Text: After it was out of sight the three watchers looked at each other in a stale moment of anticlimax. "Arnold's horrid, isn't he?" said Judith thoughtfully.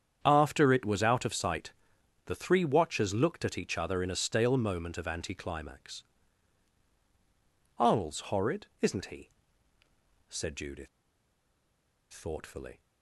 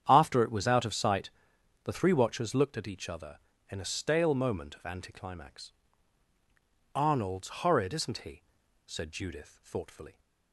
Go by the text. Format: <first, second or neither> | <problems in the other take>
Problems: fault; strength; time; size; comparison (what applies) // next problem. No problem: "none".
second | starts louder than the rest; strong; until 1.2 s; 8.5 dB; strong in the second // pauses between "sight" and "the"; noticeable; at 1.7 s; 0.54 s long; noticeable in the second // pauses between "Judith" and "thoughtfully"; strong; at 10.8 s; 1.2 s long